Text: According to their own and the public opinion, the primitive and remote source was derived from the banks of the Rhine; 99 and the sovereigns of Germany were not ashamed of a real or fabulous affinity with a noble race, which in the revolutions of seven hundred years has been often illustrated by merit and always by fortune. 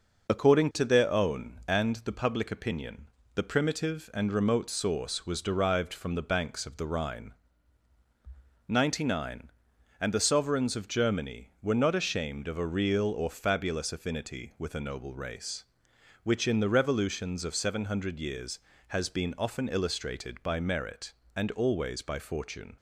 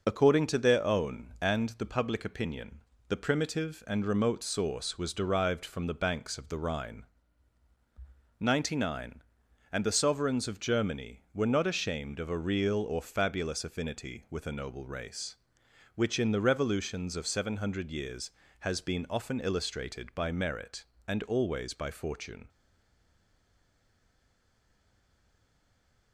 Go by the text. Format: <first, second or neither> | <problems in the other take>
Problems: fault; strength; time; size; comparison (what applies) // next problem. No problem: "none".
first | stays silent after the last word; strong; from 22.4 s on; 3.7 s long